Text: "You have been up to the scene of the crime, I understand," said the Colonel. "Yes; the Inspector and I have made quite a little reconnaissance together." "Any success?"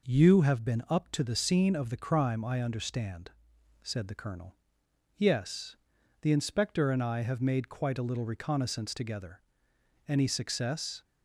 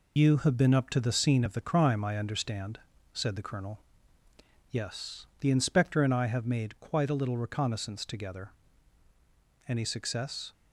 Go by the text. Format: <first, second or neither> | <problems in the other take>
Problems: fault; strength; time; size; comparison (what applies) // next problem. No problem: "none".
first | loses the start of "You"; at 0.1 s; 110 ms